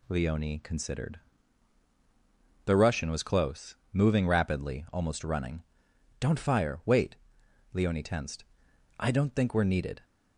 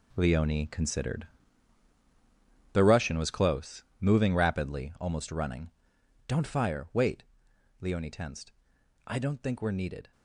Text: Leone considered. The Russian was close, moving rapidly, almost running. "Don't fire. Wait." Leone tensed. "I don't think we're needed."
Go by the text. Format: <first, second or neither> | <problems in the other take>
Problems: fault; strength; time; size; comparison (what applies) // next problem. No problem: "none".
first | gets quieter; strong; throughout; 11 dB